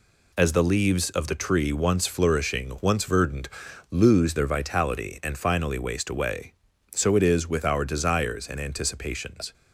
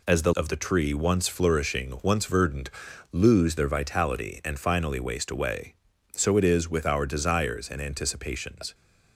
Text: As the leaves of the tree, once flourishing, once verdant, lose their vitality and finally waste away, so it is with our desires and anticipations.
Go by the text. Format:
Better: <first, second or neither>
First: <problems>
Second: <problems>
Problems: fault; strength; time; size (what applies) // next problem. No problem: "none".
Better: first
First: none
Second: skips "leaves"; at 0.3 s